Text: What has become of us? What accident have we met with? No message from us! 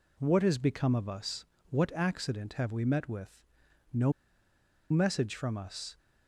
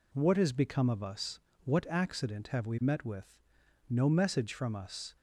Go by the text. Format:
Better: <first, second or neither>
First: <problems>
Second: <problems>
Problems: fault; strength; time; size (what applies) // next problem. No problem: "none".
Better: second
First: pauses between "No" and "message"; noticeable; at 4.1 s; 0.79 s long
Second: none